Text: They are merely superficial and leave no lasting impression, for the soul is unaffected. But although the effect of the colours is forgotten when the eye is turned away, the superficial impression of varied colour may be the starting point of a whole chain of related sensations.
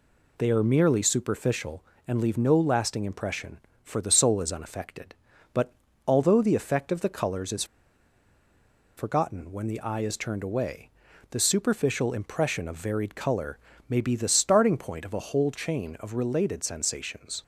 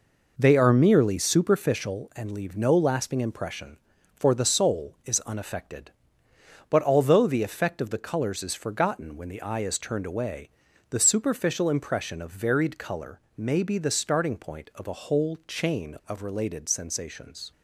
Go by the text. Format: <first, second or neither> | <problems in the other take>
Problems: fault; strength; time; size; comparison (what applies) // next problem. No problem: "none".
second | pauses between "But" and "although"; slight; at 5.7 s; 0.34 s long // pauses between "is" and "forgotten"; strong; at 7.6 s; 1.3 s long // pauses between "colour" and "may"; slight; at 13.5 s; 0.30 s long; slight in the second